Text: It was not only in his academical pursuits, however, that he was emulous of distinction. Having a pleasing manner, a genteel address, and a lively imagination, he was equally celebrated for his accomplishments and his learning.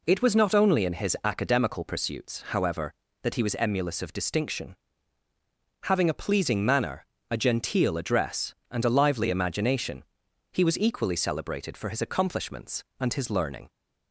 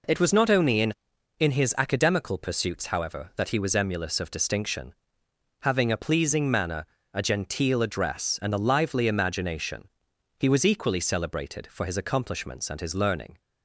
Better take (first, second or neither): first